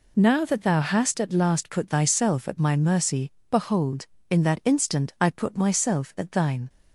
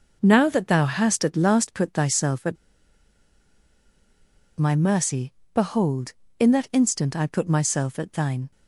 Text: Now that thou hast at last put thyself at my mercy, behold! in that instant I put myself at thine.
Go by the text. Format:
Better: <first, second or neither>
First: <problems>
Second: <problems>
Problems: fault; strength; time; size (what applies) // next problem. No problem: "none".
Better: first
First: none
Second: pauses between "at" and "my"; strong; at 2.5 s; 2.0 s long